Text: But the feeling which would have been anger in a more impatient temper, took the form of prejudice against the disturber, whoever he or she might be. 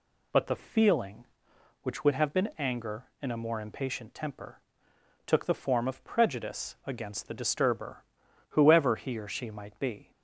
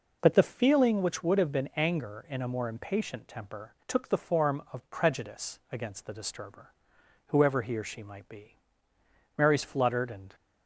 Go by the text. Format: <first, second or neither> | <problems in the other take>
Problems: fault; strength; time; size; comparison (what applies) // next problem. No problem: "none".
first | goes on to say "Mary's fluttered and"; noticeable; from 9.3 s on; 0.98 s long